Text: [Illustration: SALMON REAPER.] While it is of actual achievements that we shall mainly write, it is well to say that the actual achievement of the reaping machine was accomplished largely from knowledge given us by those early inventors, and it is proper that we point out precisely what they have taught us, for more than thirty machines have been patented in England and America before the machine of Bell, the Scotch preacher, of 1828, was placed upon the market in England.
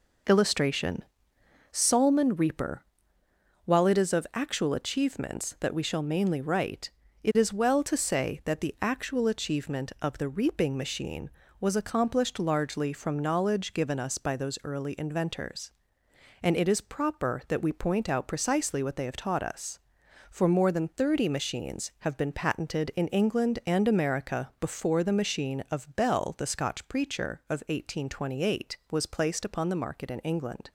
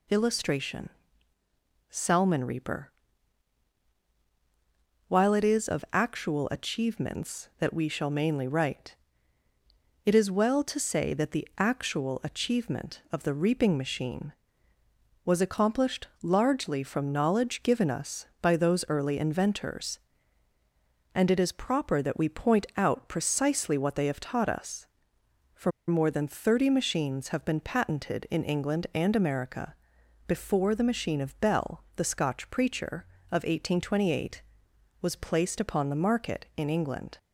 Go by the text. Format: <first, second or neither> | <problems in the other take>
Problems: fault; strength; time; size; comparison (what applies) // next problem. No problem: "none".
first | pauses between "for" and "more"; slight; at 25.7 s; 0.16 s long // pauses between "America" and "before"; noticeable; at 29.7 s; 0.54 s long